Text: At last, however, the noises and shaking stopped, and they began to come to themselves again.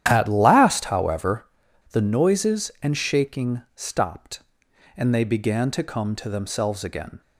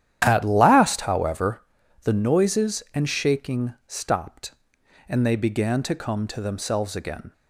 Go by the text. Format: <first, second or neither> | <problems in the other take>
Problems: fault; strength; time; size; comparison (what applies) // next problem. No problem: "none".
neither | starts louder than the rest; strong; the same in both